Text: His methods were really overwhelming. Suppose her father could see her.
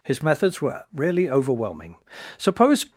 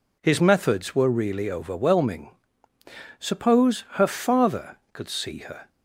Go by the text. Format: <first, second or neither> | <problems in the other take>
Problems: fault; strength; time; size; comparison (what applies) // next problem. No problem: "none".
second | stops before "her father could see her"; at 2.9 s